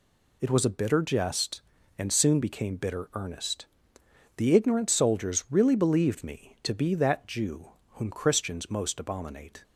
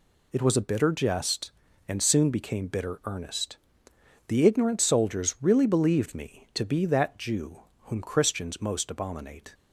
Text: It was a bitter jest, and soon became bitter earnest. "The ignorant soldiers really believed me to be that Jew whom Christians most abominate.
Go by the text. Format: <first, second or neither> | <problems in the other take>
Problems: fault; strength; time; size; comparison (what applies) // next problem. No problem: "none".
neither | pauses between "Jew" and "whom"; slight; the same in both